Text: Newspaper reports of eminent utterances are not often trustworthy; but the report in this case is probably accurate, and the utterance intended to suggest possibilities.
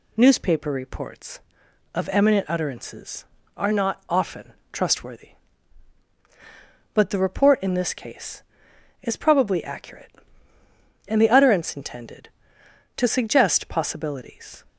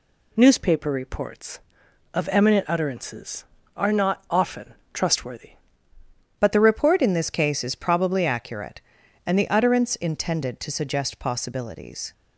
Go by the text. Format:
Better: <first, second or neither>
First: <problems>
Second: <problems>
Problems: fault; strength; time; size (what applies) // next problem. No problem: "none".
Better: first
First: pauses between "often" and "trustworthy"; slight; at 4.5 s; 0.22 s long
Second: pauses between "often" and "trustworthy"; slight; at 4.7 s; 0.22 s long // changes voice at "but"; from 6.3 s on; 5.8 s long